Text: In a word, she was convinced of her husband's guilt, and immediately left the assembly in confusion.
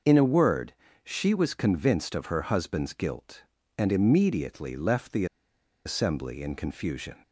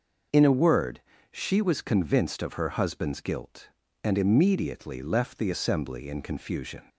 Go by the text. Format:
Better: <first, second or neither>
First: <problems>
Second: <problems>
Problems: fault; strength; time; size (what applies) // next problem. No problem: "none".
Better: second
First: starts louder than the rest; noticeable; until 1.3 s; 6 dB // pauses between "the" and "assembly"; noticeable; at 5.2 s; 0.60 s long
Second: none